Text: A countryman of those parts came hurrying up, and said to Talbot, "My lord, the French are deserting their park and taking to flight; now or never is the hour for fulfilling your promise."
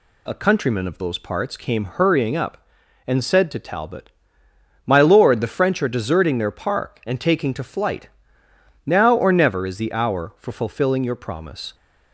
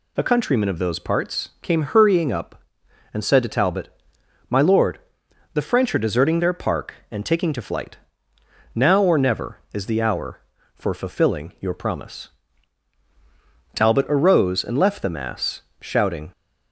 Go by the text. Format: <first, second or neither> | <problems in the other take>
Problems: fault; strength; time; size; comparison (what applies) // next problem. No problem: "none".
first | goes on to say "Talbot arose and left the mass shouting"; strong; from 13.7 s on; 2.5 s long